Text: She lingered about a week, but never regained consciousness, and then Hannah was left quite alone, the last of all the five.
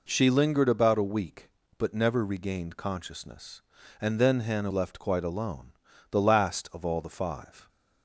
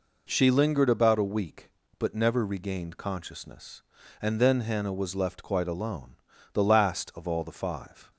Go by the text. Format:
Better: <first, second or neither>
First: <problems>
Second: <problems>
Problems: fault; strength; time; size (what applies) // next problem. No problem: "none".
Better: second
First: skips "was"; at 4.7 s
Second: none